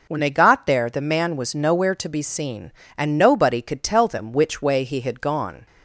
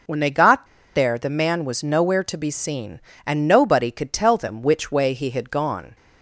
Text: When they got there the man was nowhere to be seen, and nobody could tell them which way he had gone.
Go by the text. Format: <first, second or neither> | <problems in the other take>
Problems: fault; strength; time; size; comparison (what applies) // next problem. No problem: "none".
first | pauses between "got" and "there"; slight; at 0.6 s; 0.28 s long